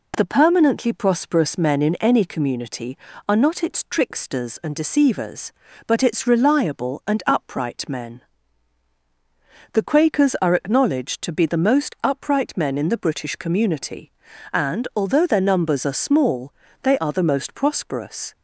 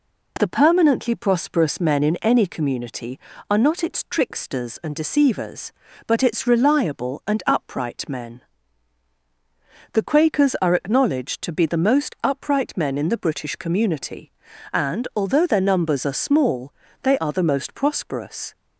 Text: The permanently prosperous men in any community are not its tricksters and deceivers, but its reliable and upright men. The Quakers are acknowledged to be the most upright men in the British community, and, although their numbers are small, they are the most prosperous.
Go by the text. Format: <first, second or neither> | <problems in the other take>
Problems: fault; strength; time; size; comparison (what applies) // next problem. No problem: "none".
neither | none